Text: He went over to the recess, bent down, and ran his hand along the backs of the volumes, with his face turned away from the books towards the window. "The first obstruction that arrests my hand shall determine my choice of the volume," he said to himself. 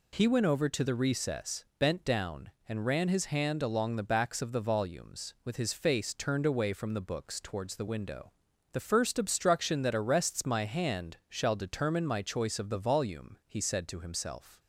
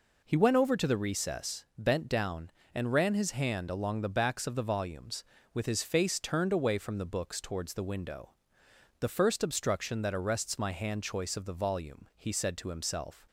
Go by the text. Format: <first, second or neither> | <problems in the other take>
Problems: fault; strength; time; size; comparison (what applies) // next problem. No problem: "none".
first | skips "shall determine my"; at 11.0 s